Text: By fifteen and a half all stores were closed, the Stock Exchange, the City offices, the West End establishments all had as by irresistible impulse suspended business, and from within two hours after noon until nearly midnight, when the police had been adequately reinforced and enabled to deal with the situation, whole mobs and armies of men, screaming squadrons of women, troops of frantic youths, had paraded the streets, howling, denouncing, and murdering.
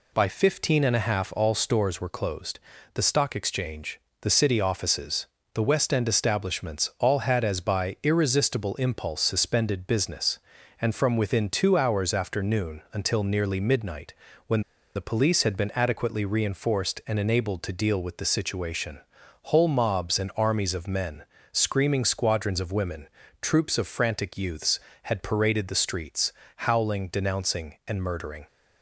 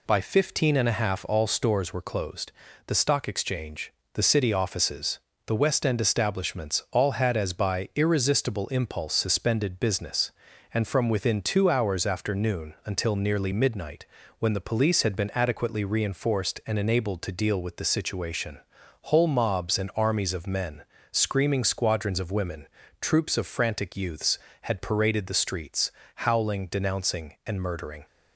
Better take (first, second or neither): second